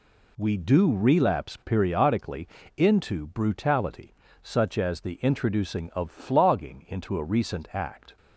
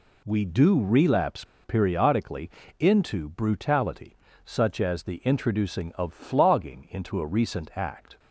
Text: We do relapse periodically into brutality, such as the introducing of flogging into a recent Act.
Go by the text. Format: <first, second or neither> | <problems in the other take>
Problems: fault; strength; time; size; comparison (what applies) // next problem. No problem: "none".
first | pauses between "relapse" and "periodically"; slight; at 1.4 s; 0.19 s long // pauses between "periodically" and "into"; slight; at 2.4 s; 0.30 s long; slight in the first